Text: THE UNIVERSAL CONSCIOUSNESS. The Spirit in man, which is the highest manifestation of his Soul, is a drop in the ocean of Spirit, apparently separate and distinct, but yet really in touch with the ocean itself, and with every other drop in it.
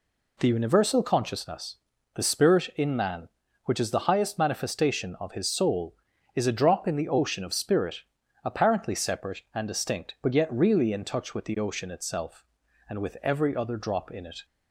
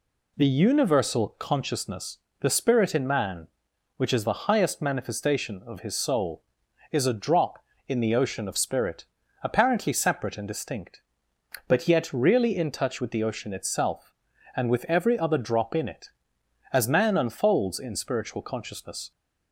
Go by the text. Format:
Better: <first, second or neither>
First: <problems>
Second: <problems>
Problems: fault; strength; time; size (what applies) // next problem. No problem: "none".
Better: first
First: none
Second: goes on to say "As man unfolds in spiritual consciousness"; strong; from 16.7 s on; 2.4 s long